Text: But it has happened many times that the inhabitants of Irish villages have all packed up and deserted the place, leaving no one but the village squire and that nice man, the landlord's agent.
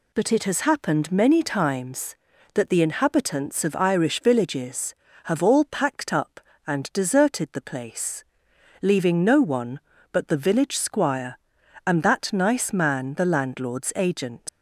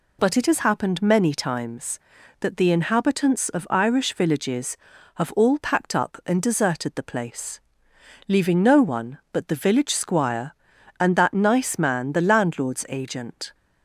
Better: second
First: leaves "agent" unfinished; at 14.4 s; 110 ms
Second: none

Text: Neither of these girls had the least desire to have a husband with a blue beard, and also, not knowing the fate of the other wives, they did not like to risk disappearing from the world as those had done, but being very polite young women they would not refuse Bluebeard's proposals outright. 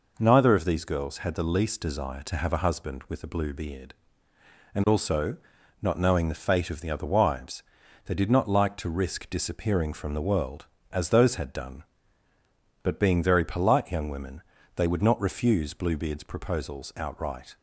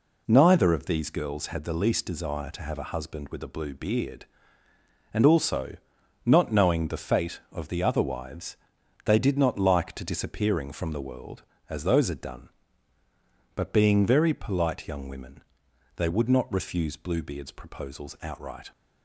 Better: first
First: pauses between "women" and "they"; slight; at 14.4 s; 0.34 s long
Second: skips "risk"; at 10.0 s // pauses between "women" and "they"; noticeable; at 15.4 s; 0.56 s long

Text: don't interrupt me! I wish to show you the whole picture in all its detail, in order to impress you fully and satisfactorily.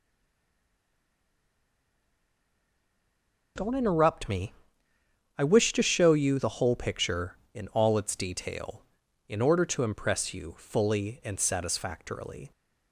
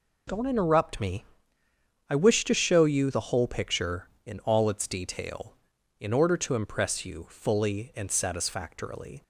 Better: second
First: stays silent before the first word; strong; until 3.5 s; 3.5 s long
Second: none

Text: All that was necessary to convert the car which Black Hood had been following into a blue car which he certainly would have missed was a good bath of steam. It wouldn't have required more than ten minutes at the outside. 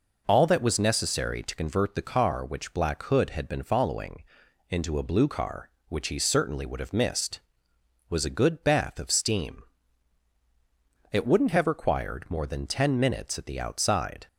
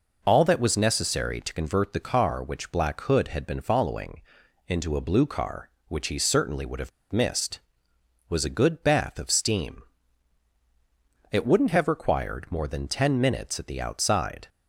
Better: first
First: pauses between "following" and "into"; noticeable; at 4.2 s; 0.48 s long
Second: pauses between "following" and "into"; noticeable; at 4.2 s; 0.48 s long // pauses between "have" and "missed"; slight; at 6.9 s; 0.22 s long

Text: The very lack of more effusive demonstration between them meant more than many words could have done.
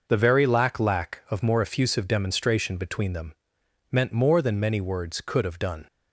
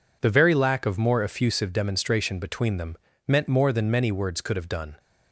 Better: second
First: says "lack" twice; at 0.7 s // pauses between "them" and "meant"; noticeable; at 3.3 s; 0.58 s long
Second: pauses between "them" and "meant"; slight; at 2.9 s; 0.28 s long

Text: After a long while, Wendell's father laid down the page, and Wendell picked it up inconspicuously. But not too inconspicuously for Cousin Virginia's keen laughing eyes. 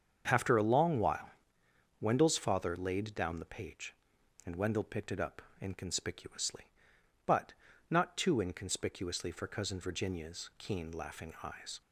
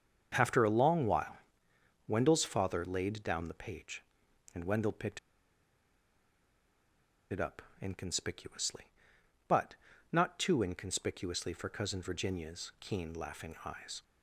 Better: first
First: starts louder than the rest; until 1.2 s; 7 dB // pauses between "up" and "inconspicuously"; slight; at 5.4 s; 0.18 s long // pauses between "But" and "not"; at 7.5 s; 0.38 s long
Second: starts louder than the rest; until 1.3 s; 7 dB // pauses between "picked" and "it"; strong; at 5.1 s; 2.1 s long // pauses between "up" and "inconspicuously"; slight; at 7.6 s; 0.18 s long // pauses between "But" and "not"; at 9.7 s; 0.38 s long

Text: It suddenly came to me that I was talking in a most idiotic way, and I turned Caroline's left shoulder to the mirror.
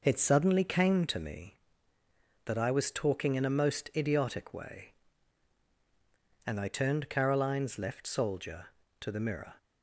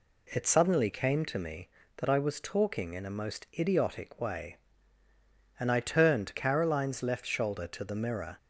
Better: second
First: says "soldier" for "shoulder"; at 8.0 s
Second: none

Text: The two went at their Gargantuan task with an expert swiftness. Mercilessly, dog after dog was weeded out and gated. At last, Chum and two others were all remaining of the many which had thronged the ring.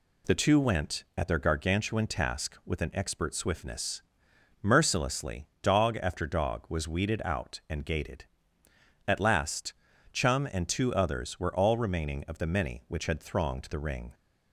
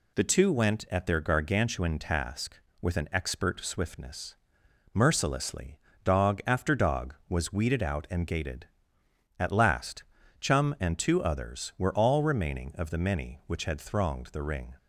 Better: neither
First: none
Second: none

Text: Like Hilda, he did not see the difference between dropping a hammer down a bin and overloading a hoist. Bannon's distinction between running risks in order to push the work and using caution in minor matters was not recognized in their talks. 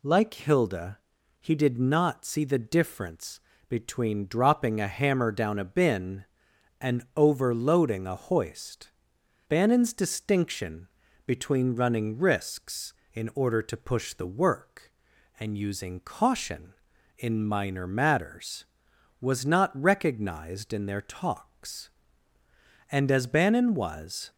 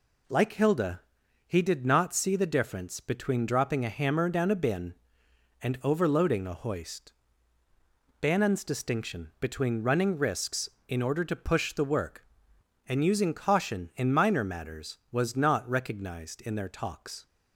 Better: second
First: pauses between "difference" and "between"; slight; at 3.4 s; 0.28 s long // pauses between "distinction" and "between"; at 10.8 s; 0.38 s long // goes on to say "And as Bannon was"; from 22.9 s on; 1.4 s long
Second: none

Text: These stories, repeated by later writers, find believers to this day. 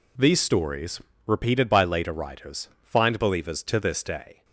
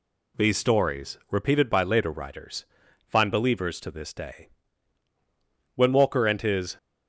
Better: first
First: none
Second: goes on to say "When Walker and his"; noticeable; from 5.7 s on; 1.0 s long

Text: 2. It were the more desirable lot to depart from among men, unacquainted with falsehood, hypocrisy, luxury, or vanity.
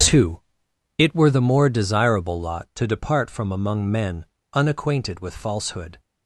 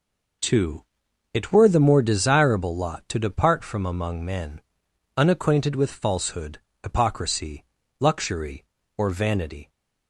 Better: second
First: starts louder than the rest; strong; until 1.6 s; 7.5 dB // stops before "hypocrisy luxury or vanity"; at 5.9 s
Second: none

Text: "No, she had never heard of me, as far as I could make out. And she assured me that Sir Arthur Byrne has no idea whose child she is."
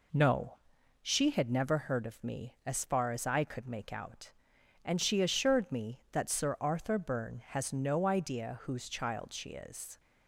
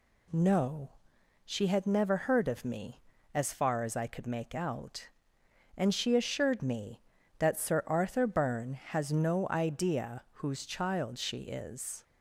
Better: neither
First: none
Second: none

